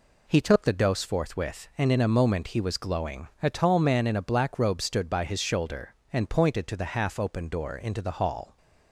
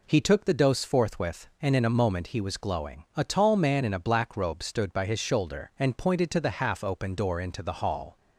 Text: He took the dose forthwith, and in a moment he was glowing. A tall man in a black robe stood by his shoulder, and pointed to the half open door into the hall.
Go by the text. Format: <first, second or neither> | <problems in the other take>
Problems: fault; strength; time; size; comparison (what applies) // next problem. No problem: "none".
neither | none